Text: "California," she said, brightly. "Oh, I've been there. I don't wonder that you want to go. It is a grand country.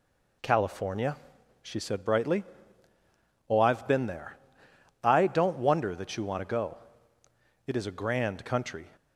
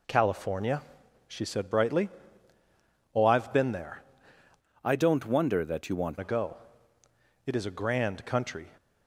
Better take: first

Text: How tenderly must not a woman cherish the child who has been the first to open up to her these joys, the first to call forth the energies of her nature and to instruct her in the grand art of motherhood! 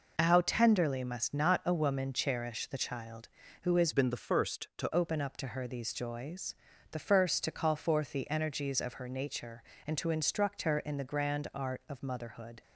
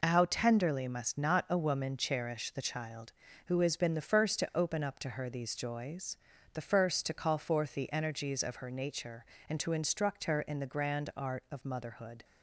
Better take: second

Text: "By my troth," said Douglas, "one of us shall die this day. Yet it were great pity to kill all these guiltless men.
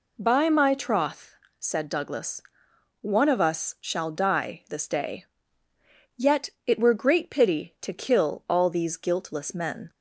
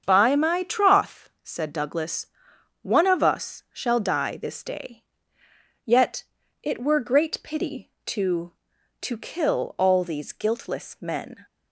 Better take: first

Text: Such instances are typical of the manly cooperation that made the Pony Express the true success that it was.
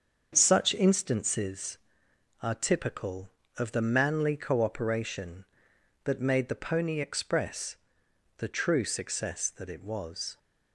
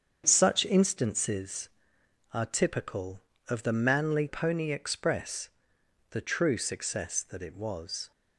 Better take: first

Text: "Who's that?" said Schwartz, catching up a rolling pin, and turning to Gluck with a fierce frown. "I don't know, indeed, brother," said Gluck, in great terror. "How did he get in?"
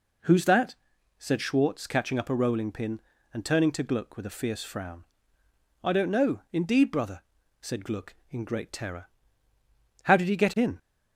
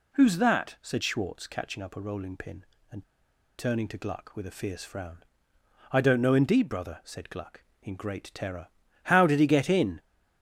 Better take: first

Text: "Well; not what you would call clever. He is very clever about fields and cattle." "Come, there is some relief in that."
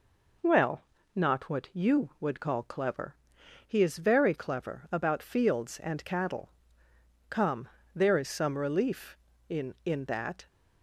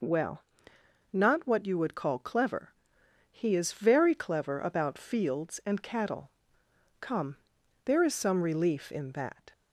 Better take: second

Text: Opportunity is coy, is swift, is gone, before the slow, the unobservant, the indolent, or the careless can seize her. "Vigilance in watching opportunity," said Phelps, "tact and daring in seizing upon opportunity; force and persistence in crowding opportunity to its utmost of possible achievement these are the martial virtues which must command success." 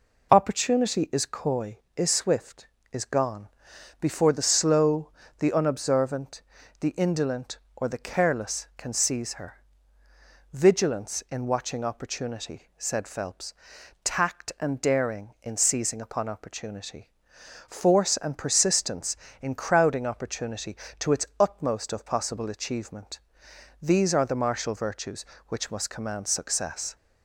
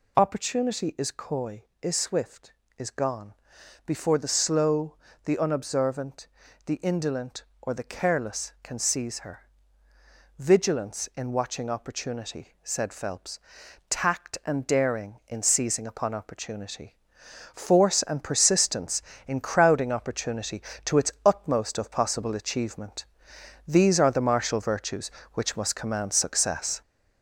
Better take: first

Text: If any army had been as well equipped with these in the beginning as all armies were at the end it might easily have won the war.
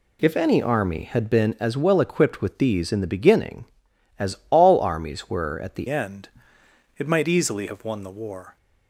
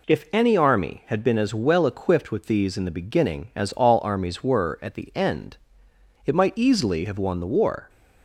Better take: second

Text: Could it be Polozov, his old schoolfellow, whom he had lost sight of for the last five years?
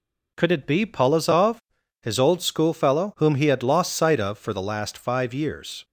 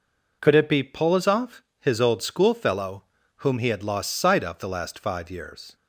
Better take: first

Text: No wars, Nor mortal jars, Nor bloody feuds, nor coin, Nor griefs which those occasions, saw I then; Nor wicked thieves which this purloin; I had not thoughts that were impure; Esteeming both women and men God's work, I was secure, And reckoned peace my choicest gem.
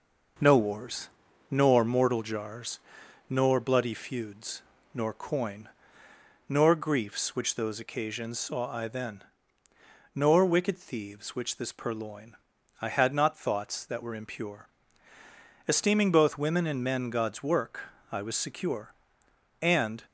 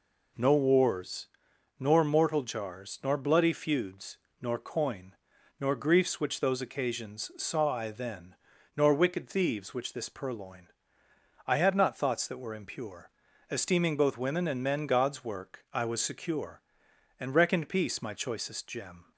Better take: second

